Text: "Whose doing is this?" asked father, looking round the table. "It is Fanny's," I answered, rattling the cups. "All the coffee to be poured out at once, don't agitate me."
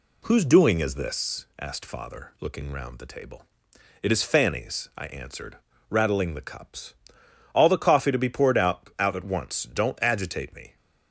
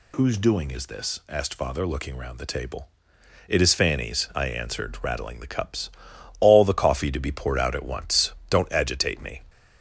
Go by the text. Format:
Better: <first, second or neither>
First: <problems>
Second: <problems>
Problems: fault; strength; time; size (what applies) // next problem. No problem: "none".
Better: second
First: says "out" twice; at 8.9 s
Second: none